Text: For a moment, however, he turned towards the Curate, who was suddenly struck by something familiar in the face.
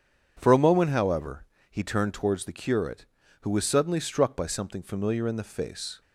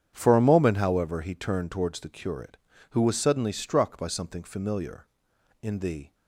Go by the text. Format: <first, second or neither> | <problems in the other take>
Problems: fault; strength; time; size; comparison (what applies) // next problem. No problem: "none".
first | starts louder than the rest; strong; until 1.1 s; 9 dB; strong in the first // stops before "face"; at 6.1 s